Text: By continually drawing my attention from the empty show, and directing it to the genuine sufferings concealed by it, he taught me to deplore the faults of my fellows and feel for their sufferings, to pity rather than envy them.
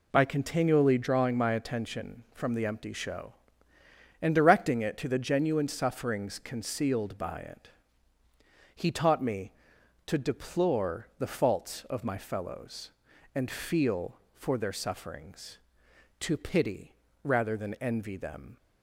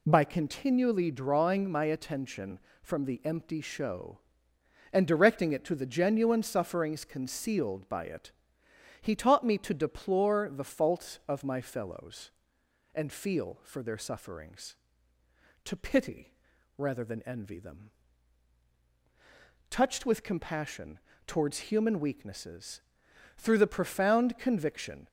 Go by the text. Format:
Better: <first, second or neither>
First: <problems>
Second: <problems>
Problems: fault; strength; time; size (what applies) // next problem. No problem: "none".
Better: first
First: pauses between "pity" and "rather"; slight; at 16.9 s; 0.30 s long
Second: pauses between "pity" and "rather"; at 16.3 s; 0.44 s long // goes on to say "Touched with compassion towards human weaknesses through the profound conviction"; strong; from 19.6 s on; 5.3 s long